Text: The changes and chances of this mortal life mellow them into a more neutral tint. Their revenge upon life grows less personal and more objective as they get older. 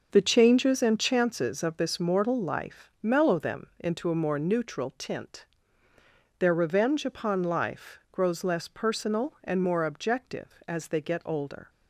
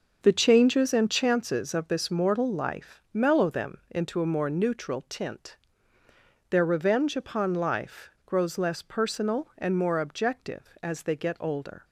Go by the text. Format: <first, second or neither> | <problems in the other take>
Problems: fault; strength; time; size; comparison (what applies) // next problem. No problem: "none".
neither | starts louder than the rest; noticeable; the same in both